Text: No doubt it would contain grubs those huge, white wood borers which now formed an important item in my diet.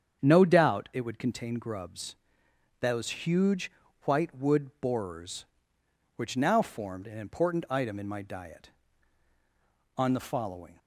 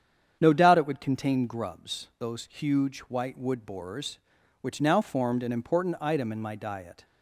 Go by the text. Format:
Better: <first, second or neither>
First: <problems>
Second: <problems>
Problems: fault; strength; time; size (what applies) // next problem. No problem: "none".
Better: second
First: starts louder than the rest; strong; until 1.2 s; 7.5 dB // pauses between "grubs" and "those"; noticeable; at 2.1 s; 0.64 s long // goes on to say "On the following"; noticeable; from 9.9 s on; 0.80 s long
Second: starts louder than the rest; strong; until 1.4 s; 8.5 dB